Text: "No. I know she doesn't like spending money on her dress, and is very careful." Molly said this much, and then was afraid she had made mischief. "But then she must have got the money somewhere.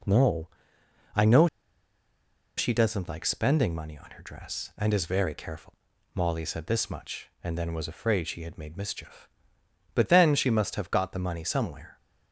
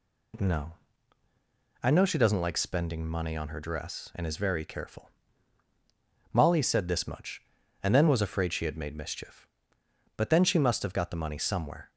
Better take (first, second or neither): second